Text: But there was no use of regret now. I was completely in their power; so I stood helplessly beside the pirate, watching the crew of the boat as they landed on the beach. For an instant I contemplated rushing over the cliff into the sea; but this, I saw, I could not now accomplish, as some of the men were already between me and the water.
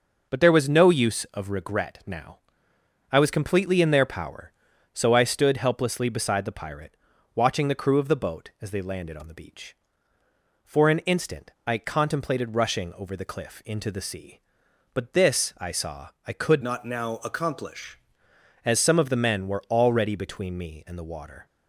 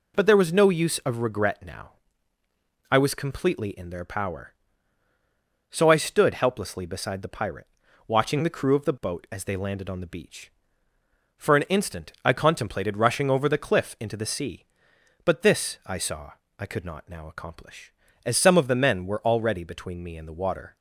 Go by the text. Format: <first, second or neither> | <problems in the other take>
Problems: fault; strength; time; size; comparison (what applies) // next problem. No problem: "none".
second | pauses between "instant" and "I"; slight; at 11.5 s; 0.16 s long // changes voice from "not" to "accomplish"; from 16.6 to 17.9 s; 1.3 s long